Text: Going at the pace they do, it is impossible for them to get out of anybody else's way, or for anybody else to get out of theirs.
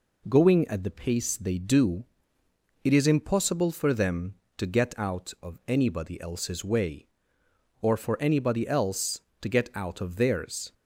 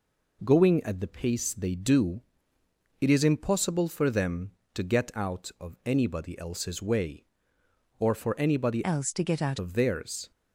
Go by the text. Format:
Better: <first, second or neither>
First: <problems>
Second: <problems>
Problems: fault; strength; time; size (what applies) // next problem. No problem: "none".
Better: first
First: none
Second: changes voice from "else" to "out"; from 8.8 to 9.5 s; 0.7 s long